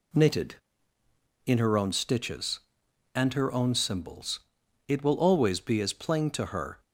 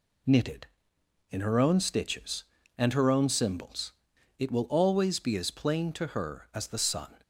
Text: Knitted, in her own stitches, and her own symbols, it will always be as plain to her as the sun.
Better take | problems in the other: second | stops before "as the sun"; at 6.8 s

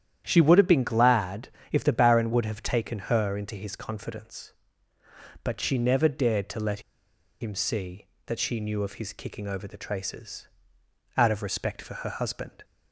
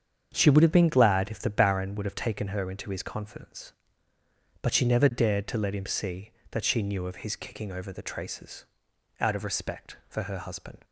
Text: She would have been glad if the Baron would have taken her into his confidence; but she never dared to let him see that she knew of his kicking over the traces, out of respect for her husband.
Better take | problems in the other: second | starts louder than the rest; strong; until 1.2 s; 10 dB; strong in the second // pauses between "glad" and "if"; slight; at 1.4 s; 0.22 s long // pauses between "let" and "him"; noticeable; at 6.7 s; 0.61 s long

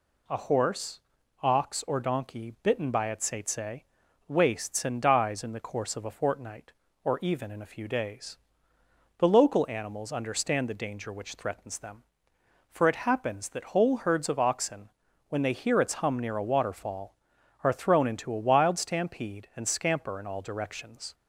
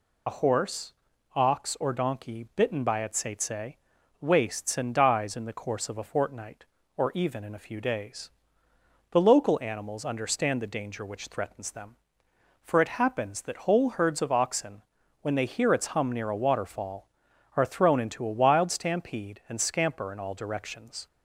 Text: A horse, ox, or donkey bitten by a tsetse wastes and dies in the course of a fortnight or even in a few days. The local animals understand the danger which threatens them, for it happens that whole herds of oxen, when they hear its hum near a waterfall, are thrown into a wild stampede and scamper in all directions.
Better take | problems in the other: first | loses the start of "A"; at 0.2 s; 60 ms // pauses between "tsetse" and "wastes"; at 3.7 s; 0.44 s long; also in the first

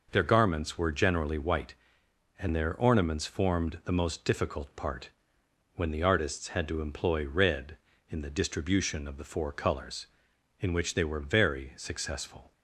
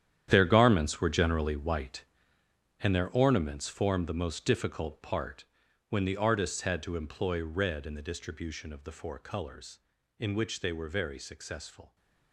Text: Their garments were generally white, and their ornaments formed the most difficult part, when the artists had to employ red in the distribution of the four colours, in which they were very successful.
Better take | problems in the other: first | gets quieter; strong; throughout; 13.5 dB

